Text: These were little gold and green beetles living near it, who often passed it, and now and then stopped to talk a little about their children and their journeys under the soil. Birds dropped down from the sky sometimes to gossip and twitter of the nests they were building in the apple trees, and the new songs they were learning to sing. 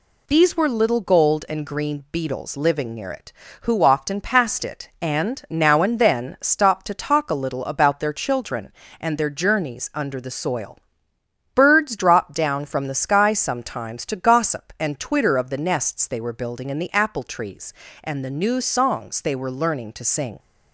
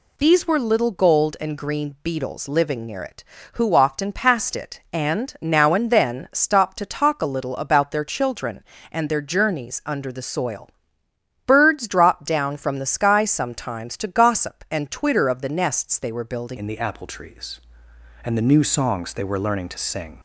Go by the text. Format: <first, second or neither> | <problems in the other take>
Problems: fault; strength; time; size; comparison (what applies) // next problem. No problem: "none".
first | changes voice at "in"; from 16.5 s on; 3.6 s long